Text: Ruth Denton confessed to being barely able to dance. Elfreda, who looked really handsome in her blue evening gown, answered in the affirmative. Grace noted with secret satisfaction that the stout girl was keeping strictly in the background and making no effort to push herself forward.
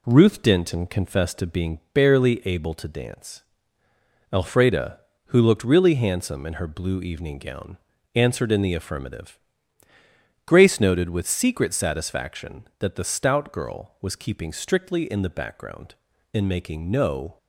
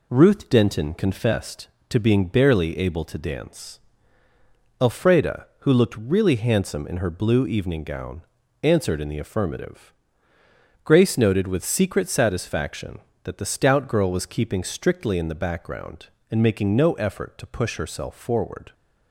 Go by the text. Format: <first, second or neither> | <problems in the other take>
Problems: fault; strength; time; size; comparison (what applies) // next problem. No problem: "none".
second | pauses between "being" and "barely"; slight; at 1.7 s; 0.16 s long // stops before "effort to push herself forward"; at 17.3 s